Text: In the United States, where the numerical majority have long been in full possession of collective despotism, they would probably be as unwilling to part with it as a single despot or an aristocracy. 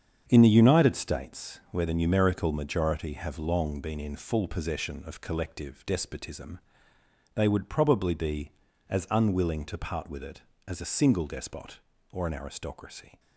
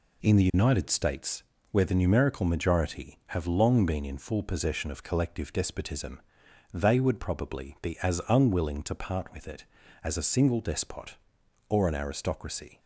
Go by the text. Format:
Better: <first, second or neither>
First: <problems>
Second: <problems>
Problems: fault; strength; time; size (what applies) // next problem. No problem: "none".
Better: second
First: gets quieter; strong; throughout; 8 dB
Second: none